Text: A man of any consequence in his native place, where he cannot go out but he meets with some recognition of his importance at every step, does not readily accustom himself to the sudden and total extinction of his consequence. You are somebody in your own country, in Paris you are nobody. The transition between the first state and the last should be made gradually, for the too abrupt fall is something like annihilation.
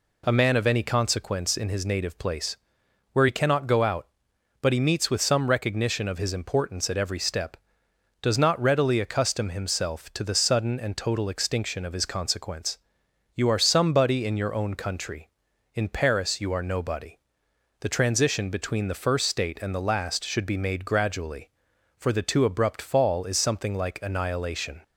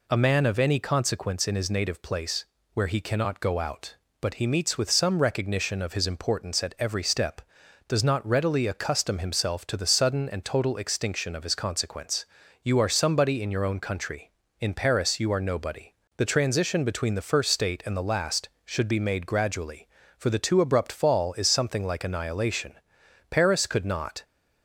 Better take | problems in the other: first | goes on to say "Paris could not"; noticeable; from 23.2 s on; 0.94 s long

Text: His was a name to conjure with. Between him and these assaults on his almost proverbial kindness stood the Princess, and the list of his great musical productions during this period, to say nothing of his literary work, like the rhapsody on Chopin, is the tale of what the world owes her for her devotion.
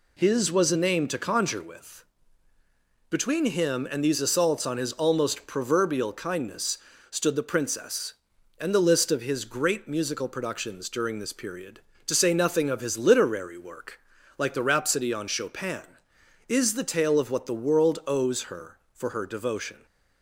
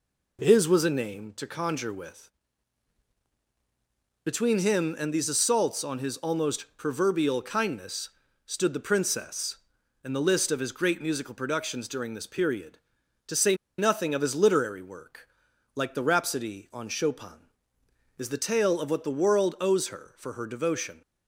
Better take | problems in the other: first | pauses between "kindness" and "stood"; at 8.0 s; 0.38 s long; slight in the first // pauses between "say" and "nothing"; slight; at 13.5 s; 0.24 s long

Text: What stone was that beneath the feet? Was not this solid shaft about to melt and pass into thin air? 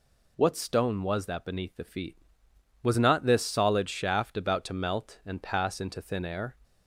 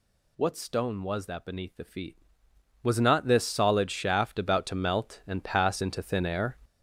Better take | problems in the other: first | gets louder; strong; throughout; 8 dB

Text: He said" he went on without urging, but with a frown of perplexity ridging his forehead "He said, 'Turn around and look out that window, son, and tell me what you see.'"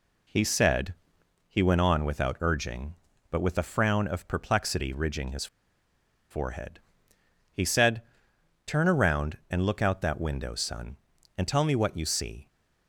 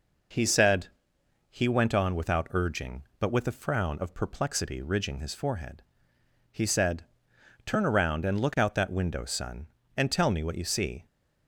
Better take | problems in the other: second | pauses between "said" and "he"; noticeable; at 0.9 s; 0.54 s long; noticeable in the second // pauses between "his" and "forehead"; noticeable; at 5.4 s; 0.84 s long // pauses between "forehead" and "He"; noticeable; at 6.7 s; 0.74 s long; noticeable in the second

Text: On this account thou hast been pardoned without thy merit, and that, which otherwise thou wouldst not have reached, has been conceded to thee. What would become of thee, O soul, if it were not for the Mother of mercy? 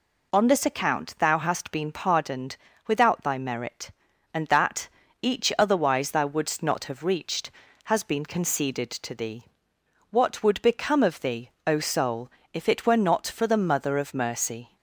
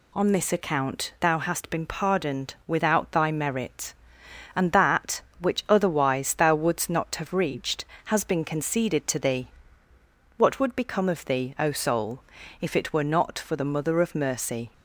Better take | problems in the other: second | pauses between "pardoned" and "without"; slight; at 2.5 s; 0.28 s long // says "each" for "which"; at 5.2 s

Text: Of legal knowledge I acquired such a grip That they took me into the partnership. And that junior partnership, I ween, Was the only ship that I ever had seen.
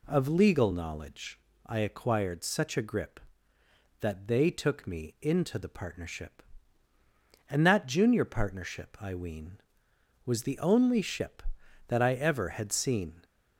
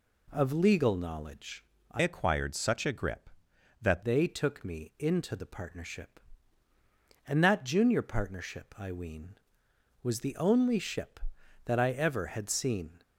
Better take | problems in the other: first | pauses between "knowledge" and "I"; slight; at 1.6 s; 0.26 s long; slight in the first // changes voice from "acquired" to "That"; from 2.0 to 4.0 s; 2.0 s long

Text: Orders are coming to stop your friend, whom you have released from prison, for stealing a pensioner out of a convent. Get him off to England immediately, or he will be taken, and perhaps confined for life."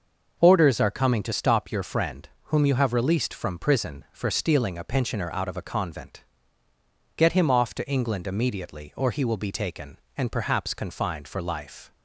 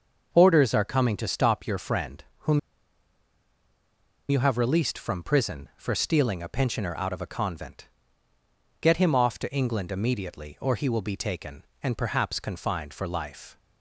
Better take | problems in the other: first | starts louder than the rest; noticeable; until 1.3 s; 6 dB; noticeable in the first // pauses between "whom" and "you"; strong; at 2.5 s; 1.7 s long

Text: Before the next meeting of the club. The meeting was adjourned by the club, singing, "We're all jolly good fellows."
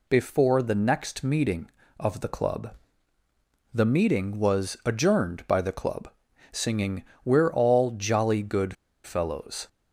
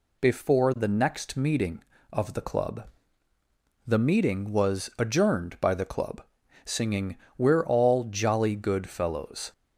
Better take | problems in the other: second | pauses between "good" and "fellows"; slight; at 8.7 s; 0.29 s long

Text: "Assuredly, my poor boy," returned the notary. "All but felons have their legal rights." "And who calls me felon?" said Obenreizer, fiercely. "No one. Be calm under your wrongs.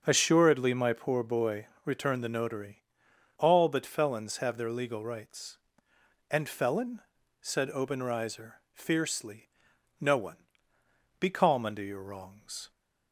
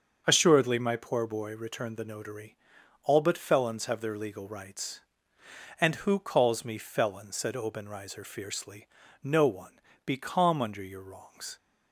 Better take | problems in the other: second | starts louder than the rest; strong; until 1.0 s; 7.5 dB; also in the second // skips "who calls me"; at 6.4 s

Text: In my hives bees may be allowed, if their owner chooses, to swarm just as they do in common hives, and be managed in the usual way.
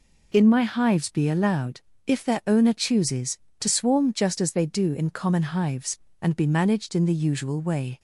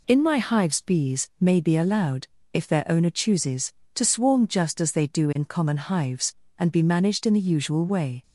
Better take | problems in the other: second | skips "bees may"; at 1.1 s

